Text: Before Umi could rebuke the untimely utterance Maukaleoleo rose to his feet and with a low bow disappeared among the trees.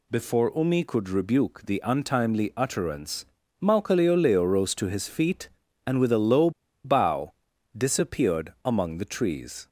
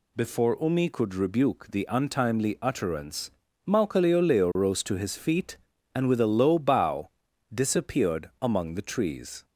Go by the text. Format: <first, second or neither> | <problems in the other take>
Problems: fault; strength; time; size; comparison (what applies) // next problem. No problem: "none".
second | pauses between "utterance" and "Maukaleoleo"; at 3.2 s; 0.38 s long; also in the second // pauses between "low" and "bow"; slight; at 6.5 s; 0.34 s long // pauses between "bow" and "disappeared"; noticeable; at 7.3 s; 0.46 s long; noticeable in the second